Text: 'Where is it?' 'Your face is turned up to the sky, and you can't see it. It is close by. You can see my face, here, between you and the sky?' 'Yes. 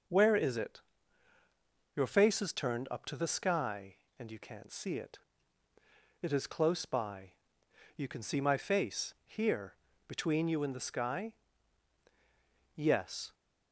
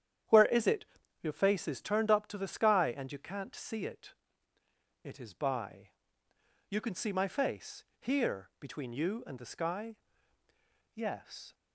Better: first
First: none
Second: starts louder than the rest; strong; until 1.6 s; 9.5 dB // skips "close"; at 5.3 s

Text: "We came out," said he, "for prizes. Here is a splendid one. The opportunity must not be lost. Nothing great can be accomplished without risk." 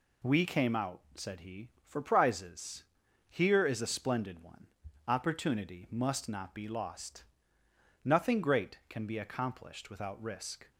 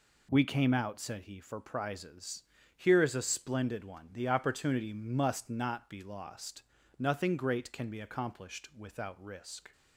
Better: second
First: skips "The"; at 4.8 s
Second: none

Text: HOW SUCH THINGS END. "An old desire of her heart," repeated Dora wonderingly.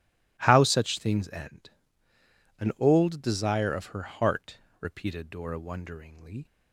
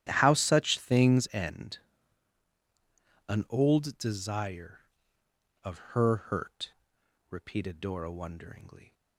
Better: first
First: none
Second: starts louder than the rest; strong; until 1.0 s; 11.5 dB // says "hurt" for "heart"; at 6.1 s

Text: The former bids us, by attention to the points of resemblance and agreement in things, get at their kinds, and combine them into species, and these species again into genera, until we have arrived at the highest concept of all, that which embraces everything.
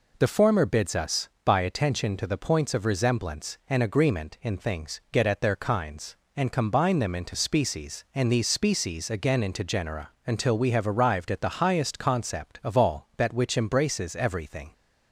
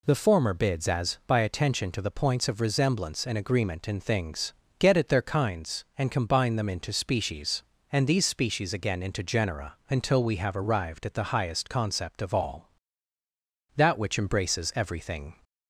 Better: first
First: none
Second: says "as" for "us"; at 0.8 s

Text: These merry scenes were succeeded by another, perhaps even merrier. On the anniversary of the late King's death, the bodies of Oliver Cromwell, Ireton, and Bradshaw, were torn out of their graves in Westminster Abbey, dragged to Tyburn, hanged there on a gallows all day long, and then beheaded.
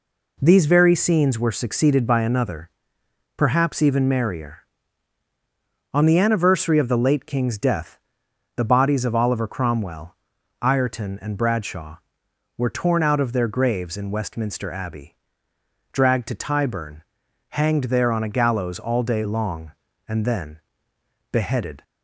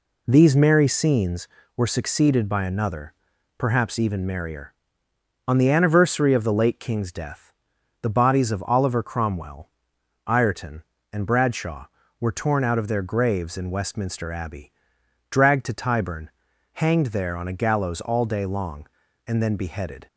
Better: second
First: says "very" for "merry"; at 0.6 s // pauses between "then" and "beheaded"; noticeable; at 20.6 s; 0.72 s long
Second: none

